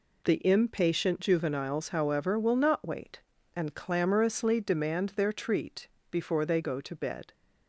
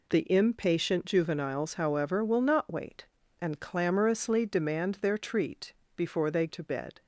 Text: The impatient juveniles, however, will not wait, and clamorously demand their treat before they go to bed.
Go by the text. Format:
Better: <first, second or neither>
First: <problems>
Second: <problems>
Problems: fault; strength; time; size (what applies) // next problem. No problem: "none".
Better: first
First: pauses between "treat" and "before"; slight; at 5.8 s; 0.24 s long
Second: pauses between "treat" and "before"; slight; at 5.7 s; 0.24 s long // skips "go"; at 6.4 s